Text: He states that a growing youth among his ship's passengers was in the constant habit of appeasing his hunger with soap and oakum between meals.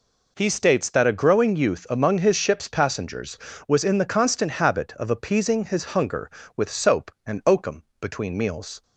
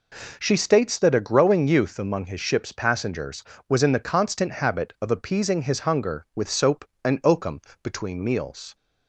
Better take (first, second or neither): first